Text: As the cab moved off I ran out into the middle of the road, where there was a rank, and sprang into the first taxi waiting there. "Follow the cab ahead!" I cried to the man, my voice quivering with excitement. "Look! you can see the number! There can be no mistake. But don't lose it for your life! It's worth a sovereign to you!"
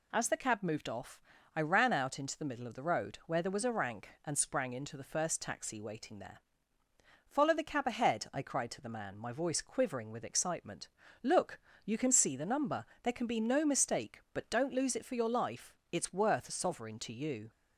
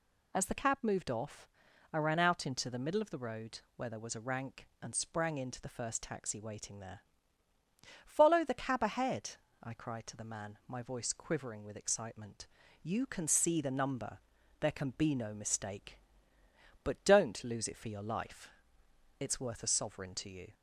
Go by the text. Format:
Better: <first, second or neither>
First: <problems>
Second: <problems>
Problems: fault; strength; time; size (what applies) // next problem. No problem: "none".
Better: first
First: pauses between "off" and "I"; slight; at 1.2 s; 0.34 s long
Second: pauses between "off" and "I"; noticeable; at 1.4 s; 0.46 s long // skips "Look"; at 12.6 s